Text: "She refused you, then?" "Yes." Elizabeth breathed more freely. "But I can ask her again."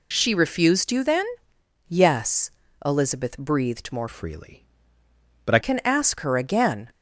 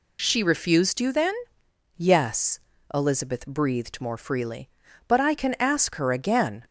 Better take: second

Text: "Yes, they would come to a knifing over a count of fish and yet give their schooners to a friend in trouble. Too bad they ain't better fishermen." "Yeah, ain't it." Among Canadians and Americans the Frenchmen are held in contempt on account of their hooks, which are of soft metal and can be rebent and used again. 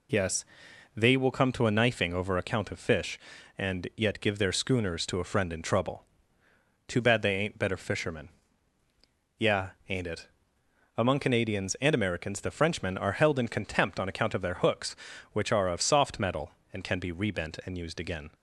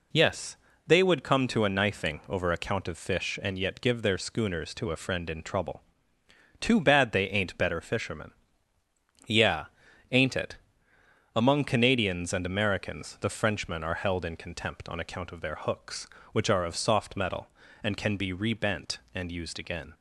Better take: second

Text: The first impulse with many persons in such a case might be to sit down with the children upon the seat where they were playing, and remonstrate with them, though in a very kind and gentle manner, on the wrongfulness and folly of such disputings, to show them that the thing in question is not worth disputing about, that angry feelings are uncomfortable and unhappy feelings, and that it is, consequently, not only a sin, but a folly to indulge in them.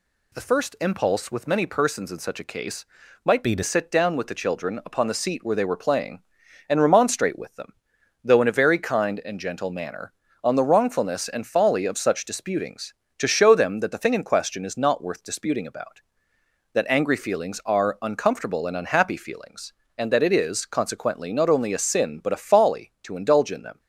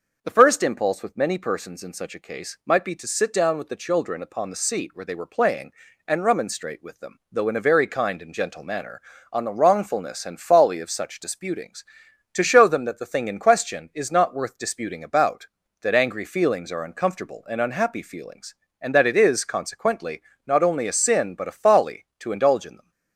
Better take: second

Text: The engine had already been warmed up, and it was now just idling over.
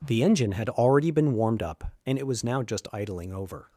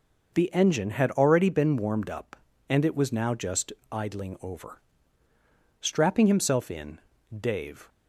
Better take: first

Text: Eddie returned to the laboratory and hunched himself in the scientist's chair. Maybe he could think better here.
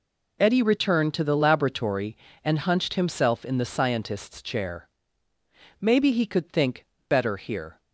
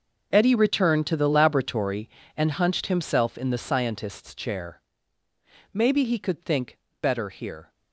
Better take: first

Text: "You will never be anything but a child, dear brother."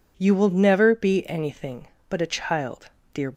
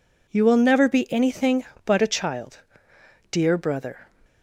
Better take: second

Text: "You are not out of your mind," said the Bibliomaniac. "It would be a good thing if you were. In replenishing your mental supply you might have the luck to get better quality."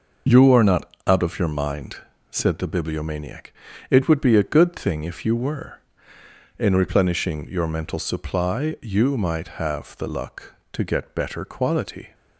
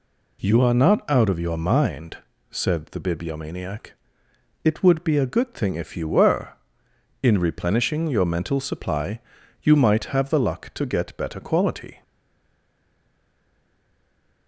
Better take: first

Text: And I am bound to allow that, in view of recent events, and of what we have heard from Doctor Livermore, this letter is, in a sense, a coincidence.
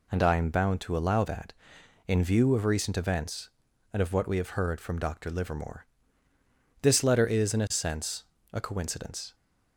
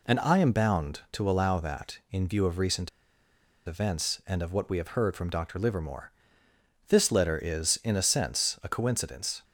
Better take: first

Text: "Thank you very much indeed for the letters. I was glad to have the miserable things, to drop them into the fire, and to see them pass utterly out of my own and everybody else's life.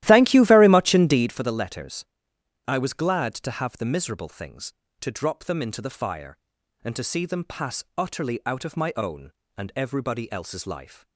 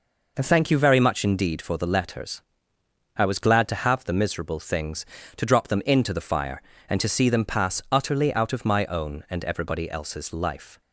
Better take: second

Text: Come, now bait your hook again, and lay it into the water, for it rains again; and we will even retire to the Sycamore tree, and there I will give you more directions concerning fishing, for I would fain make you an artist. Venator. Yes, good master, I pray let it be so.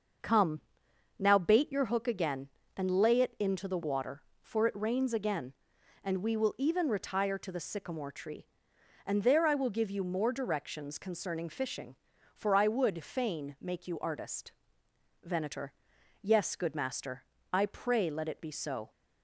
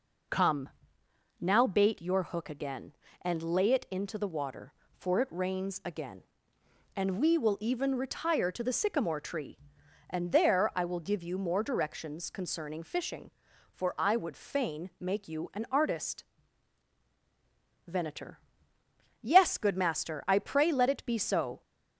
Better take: second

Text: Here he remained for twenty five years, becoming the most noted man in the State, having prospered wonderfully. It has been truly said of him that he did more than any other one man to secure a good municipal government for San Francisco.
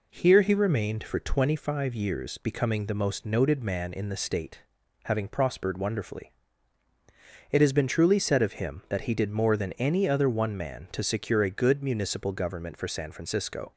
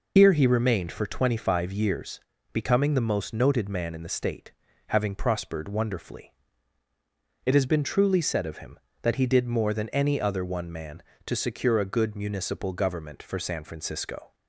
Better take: first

